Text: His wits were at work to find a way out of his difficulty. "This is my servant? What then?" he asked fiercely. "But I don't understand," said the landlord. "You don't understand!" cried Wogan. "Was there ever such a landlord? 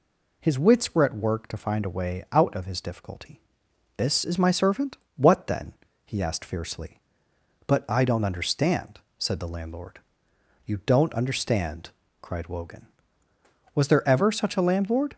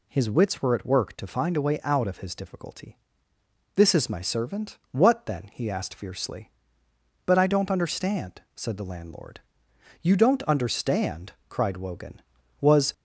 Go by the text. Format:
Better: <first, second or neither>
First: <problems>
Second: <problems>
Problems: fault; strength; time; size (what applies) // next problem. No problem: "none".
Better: first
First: none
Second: stops before "there ever such a landlord"; at 12.9 s